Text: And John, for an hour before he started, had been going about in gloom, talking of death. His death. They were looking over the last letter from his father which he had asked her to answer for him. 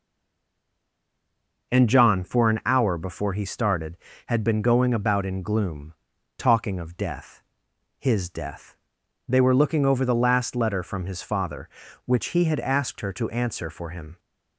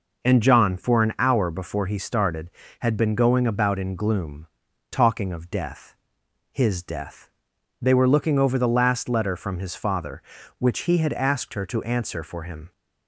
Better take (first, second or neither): second